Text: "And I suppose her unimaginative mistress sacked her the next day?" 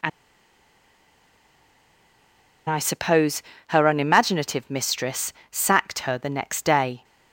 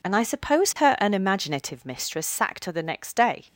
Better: second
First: pauses between "And" and "I"; strong; at 0.0 s; 2.5 s long // pauses between "suppose" and "her"; slight; at 3.4 s; 0.26 s long // pauses between "mistress" and "sacked"; slight; at 5.3 s; 0.16 s long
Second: none

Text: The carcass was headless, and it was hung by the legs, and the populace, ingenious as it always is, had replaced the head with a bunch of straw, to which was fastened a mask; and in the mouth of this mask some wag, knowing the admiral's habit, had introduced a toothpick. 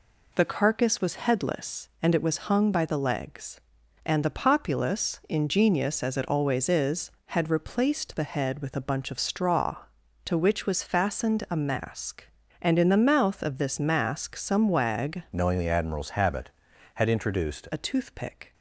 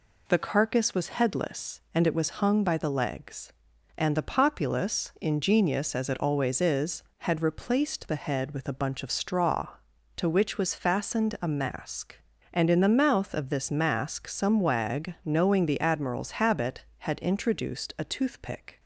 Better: second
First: changes voice from "knowing" to "introduced"; from 15.3 to 17.6 s; 2.3 s long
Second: none

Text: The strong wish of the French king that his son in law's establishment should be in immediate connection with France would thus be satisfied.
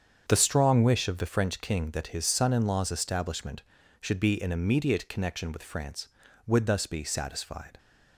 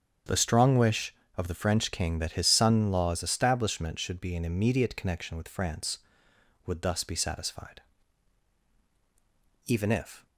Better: first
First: starts louder than the rest; strong; until 1.3 s; 7.5 dB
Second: starts louder than the rest; strong; until 1.5 s; 7.5 dB // goes on to say "Even if"; noticeable; from 9.6 s on; 0.62 s long

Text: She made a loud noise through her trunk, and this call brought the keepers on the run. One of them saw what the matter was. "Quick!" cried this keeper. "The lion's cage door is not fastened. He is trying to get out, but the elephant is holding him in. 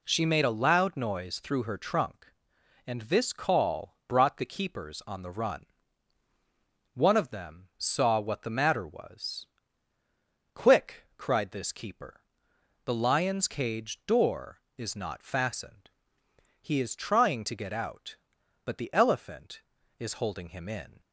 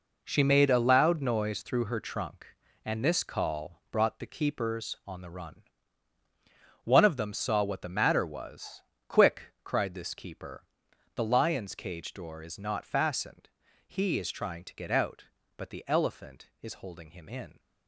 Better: first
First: none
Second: gets quieter; strong; throughout; 10 dB

